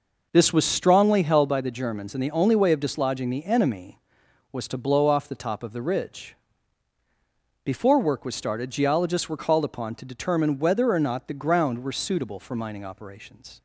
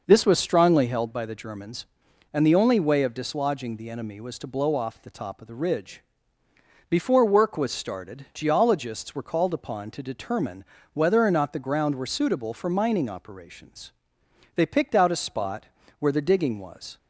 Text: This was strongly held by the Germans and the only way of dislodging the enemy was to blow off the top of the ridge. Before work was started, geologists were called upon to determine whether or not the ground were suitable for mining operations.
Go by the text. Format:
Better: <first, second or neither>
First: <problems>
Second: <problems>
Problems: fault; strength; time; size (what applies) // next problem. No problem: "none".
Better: first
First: none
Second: pauses between "determine" and "whether"; slight; at 10.6 s; 0.30 s long // goes on to say "They picked out a spot where the digging was"; strong; from 14.5 s on; 2.4 s long